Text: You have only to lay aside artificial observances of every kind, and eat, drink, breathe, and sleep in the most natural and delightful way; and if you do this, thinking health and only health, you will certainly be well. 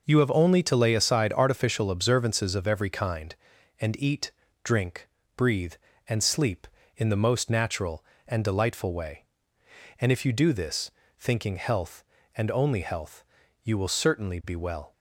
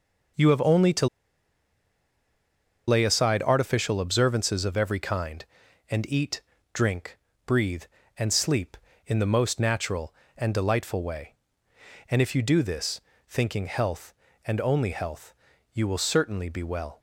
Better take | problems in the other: first | pauses between "to" and "lay"; strong; at 1.0 s; 1.8 s long

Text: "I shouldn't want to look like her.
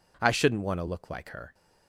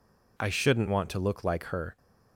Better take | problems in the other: neither | none

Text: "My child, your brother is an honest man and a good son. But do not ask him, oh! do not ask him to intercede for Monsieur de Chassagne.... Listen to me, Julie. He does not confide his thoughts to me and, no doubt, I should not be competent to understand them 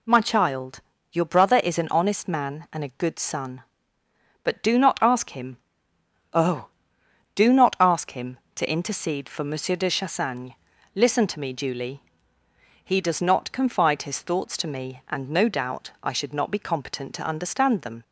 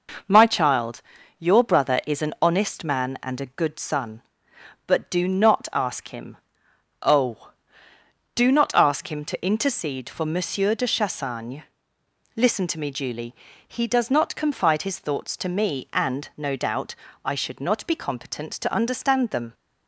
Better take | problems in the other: neither | none

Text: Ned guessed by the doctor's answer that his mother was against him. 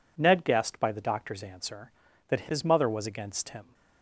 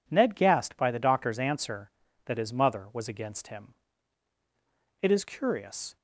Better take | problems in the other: first | goes on to say "It is curious"; noticeable; from 5.0 s on; 0.94 s long

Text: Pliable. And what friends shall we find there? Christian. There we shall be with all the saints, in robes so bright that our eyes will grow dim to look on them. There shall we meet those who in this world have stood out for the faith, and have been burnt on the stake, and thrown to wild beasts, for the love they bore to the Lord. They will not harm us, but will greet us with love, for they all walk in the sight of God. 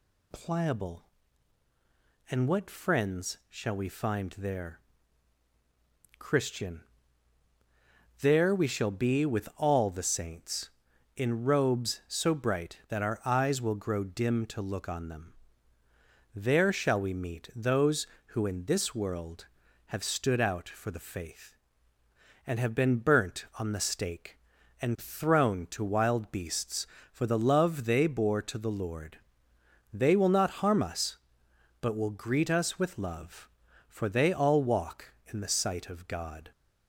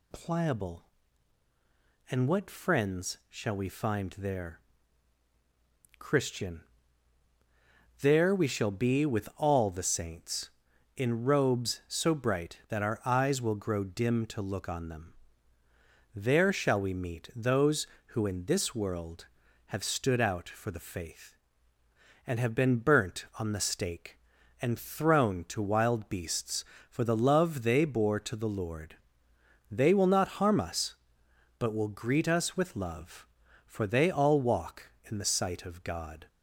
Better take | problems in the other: neither | none

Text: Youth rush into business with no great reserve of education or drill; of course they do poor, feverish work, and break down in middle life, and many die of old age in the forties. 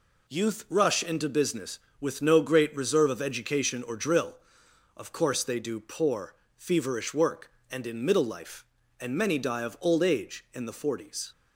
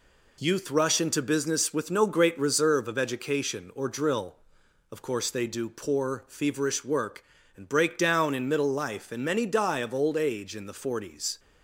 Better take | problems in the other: second | skips "break down"; at 7.8 s

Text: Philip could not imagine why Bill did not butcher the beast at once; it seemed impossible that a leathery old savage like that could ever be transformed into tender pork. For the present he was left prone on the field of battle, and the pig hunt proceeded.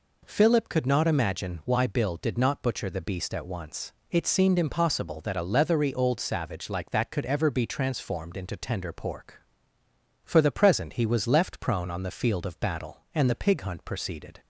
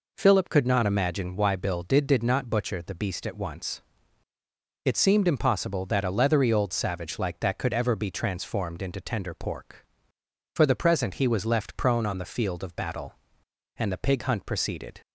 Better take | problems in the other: first | says "did" twice; at 2.0 s

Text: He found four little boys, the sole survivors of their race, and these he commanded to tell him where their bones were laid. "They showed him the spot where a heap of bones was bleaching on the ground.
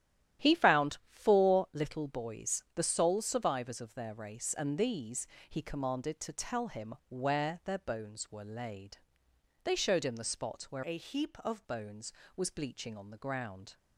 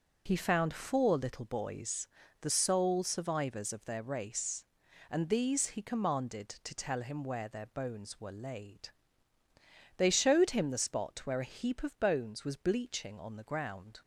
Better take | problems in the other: second | starts louder than the rest; strong; until 1.5 s; 11 dB // pauses between "these" and "he"; slight; at 5.2 s; 0.24 s long // pauses between "him" and "where"; slight; at 6.9 s; 0.16 s long // changes voice from "a" to "of"; from 10.8 to 11.6 s; 0.8 s long

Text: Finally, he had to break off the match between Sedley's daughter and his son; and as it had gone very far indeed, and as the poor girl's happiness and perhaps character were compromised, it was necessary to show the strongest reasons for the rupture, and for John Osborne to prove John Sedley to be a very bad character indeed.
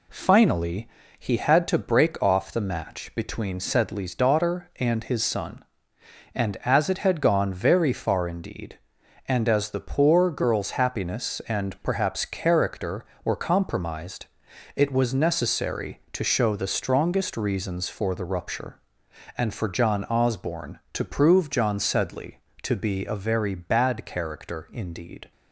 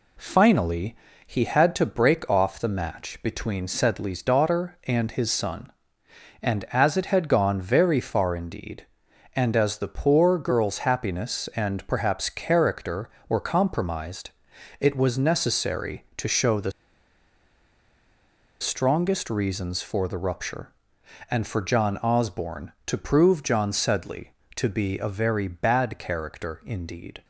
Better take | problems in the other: first | pauses between "the" and "strongest"; strong; at 16.7 s; 1.8 s long

